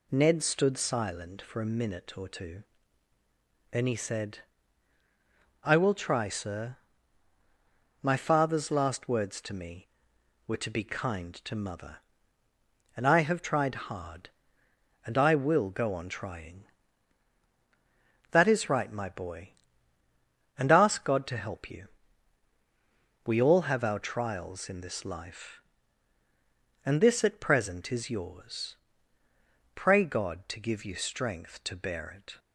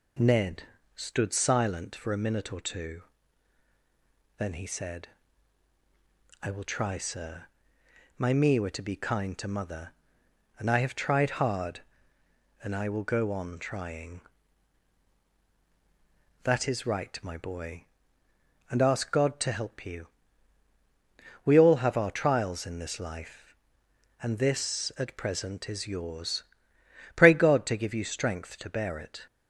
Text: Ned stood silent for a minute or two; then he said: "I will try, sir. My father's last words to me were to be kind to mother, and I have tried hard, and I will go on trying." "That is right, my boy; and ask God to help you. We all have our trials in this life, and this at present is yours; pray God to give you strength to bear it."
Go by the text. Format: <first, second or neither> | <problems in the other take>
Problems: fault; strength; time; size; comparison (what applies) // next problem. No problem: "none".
first | pauses between "Ned" and "stood"; slight; at 0.6 s; 0.32 s long // skips "father's last words to"; at 8.3 s